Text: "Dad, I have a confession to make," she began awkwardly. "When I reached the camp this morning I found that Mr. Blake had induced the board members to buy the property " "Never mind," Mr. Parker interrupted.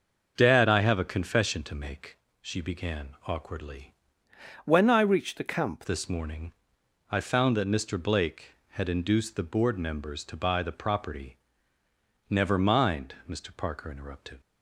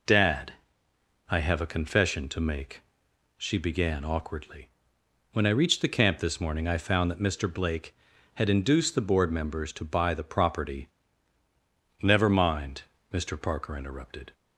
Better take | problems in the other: second | starts louder than the rest; until 1.3 s; 6 dB // changes voice from "When" to "camp"; from 4.6 to 5.8 s; 1.2 s long // pauses between "morning" and "I"; noticeable; at 6.5 s; 0.56 s long

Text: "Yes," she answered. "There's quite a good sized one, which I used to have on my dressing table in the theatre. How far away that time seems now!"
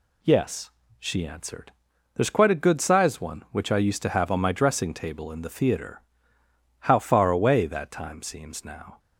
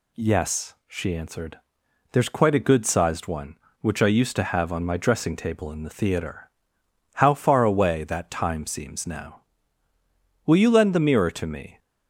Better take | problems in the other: first | goes on to say "Will you lend the mirror to me"; from 10.4 s on; 1.3 s long

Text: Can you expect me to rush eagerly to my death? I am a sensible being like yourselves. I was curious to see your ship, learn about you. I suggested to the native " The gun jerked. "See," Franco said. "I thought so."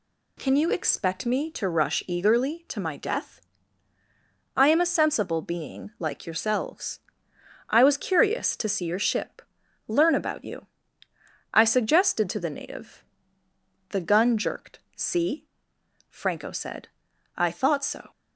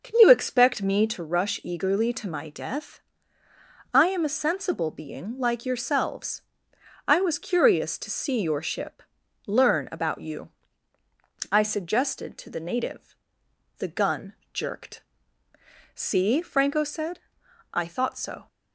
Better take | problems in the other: first | starts louder than the rest; noticeable; until 1.2 s; 5.5 dB // pauses between "gun" and "jerked"; slight; at 14.3 s; 0.18 s long

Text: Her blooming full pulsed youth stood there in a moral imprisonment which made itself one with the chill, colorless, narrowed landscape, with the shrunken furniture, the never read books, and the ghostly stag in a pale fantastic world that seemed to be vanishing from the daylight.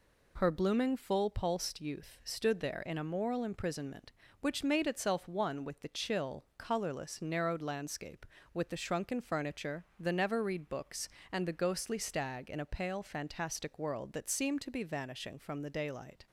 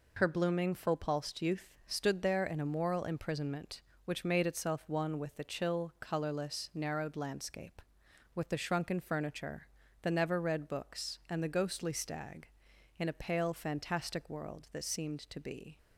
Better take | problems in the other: first | pauses between "youth" and "stood"; slight; at 1.6 s; 0.16 s long // stops before "vanishing from the daylight"; at 15.7 s

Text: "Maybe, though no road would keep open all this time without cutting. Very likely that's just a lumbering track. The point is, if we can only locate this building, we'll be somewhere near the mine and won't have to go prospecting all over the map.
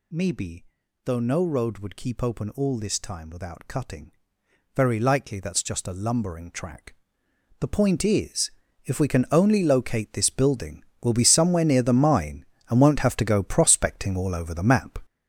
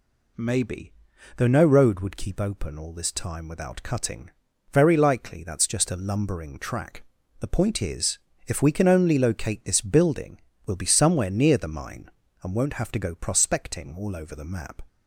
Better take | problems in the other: second | gets louder; strong; throughout; 9 dB

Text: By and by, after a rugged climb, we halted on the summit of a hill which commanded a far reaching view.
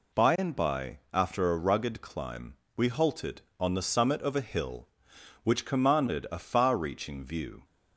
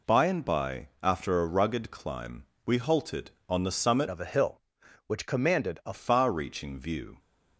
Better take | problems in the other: first | changes voice from "of" to "a"; from 4.0 to 5.9 s; 1.9 s long

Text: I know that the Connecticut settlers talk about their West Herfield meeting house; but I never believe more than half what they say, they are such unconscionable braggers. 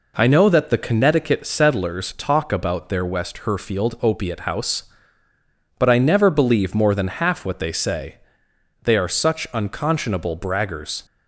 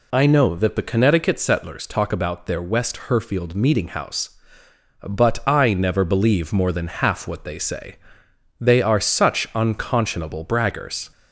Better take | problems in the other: second | says "opiate" for "meeting"; at 4.0 s

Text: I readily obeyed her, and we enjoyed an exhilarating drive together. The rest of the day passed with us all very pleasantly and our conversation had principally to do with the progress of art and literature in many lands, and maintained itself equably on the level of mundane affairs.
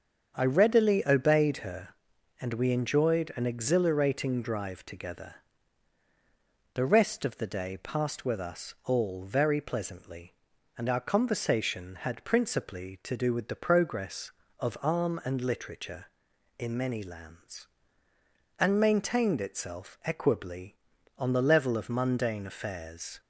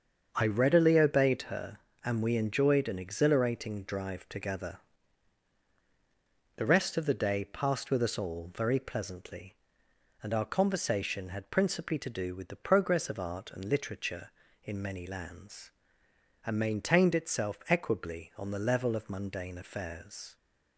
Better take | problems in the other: second | starts louder than the rest; strong; until 1.3 s; 7 dB; also in the second // says "arm" for "art"; at 14.8 s

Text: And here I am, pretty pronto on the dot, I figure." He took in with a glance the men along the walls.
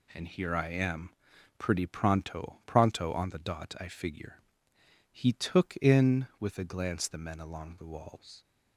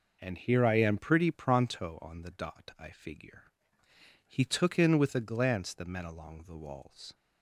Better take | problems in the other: second | says "pronto" twice; at 2.6 s

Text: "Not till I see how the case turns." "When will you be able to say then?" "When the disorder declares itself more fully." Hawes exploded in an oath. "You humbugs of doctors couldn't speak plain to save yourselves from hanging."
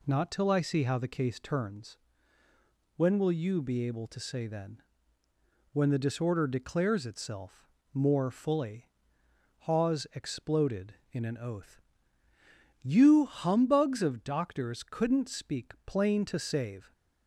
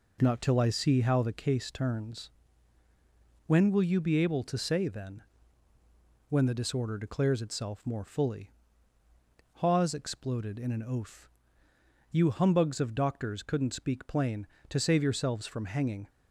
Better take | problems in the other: second | pauses between "itself" and "more"; slight; at 7.6 s; 0.26 s long // stops before "yourselves from hanging"; at 16.9 s

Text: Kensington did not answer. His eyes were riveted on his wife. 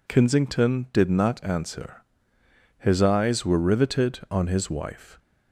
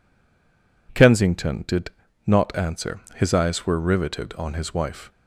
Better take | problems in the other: first | stays silent before the first word; slight; until 0.8 s; 0.8 s long // pauses between "did" and "not"; slight; at 1.9 s; 0.36 s long

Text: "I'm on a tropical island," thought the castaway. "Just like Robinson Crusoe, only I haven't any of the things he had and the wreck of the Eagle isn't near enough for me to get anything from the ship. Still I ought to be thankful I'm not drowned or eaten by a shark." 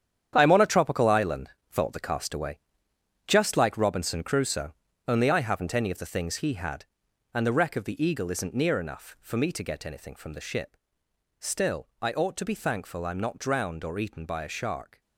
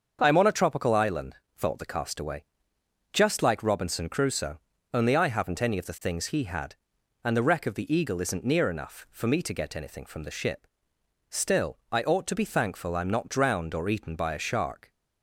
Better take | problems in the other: second | gets quieter; strong; throughout; 10 dB // starts louder than the rest; strong; until 1.3 s; 9 dB; also in the second

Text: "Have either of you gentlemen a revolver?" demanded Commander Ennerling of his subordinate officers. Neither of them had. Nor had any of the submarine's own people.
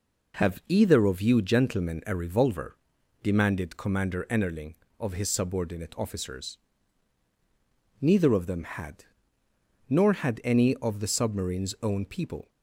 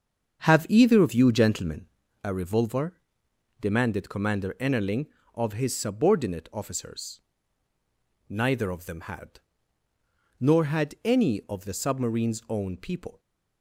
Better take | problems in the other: first | starts louder than the rest; strong; until 2.0 s; 7.5 dB // pauses between "gentlemen" and "a"; at 1.8 s; 0.38 s long

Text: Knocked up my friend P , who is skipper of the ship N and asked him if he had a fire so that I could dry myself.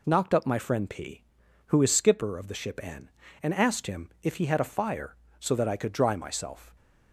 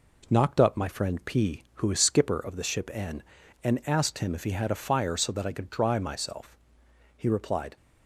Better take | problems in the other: first | goes on to say "He replied"; from 7.1 s on; 0.58 s long

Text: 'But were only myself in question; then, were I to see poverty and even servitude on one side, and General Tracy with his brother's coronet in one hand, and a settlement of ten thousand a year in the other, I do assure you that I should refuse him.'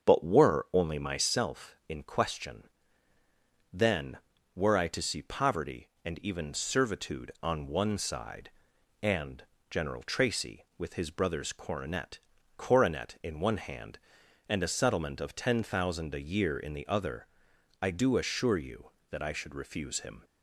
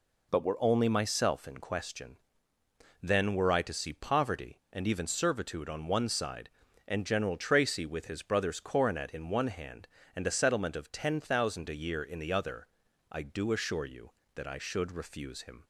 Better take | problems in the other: second | starts louder than the rest; until 1.1 s; 6.5 dB // pauses between "and" and "General"; slight; at 9.4 s; 0.26 s long // says "coronet" twice; at 12.5 s

